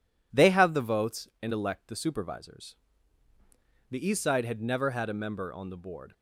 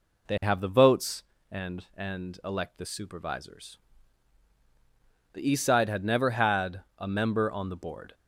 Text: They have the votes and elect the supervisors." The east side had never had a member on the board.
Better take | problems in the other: first | says "and" twice; at 1.9 s // pauses between "had" and "a"; slight; at 6.8 s; 0.16 s long

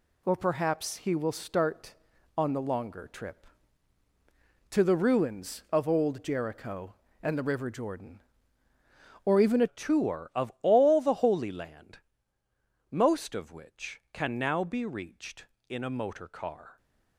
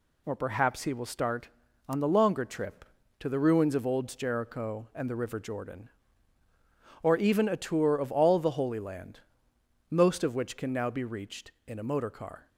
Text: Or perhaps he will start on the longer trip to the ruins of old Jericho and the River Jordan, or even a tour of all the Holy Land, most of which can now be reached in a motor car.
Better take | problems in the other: second | changes voice at "tour"; from 9.6 s on; 7.1 s long

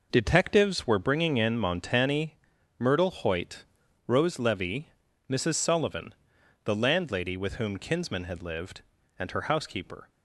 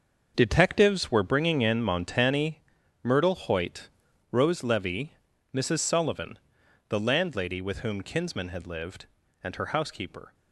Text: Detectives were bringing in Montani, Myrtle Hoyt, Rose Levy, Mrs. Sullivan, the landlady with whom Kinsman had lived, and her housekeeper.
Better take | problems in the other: first | gets quieter; strong; throughout; 10.5 dB

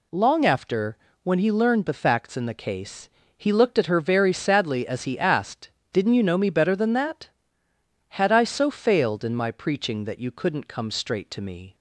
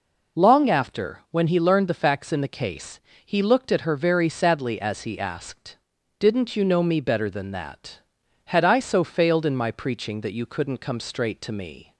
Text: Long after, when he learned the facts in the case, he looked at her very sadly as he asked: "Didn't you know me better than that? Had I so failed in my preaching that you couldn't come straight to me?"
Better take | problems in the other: neither | none

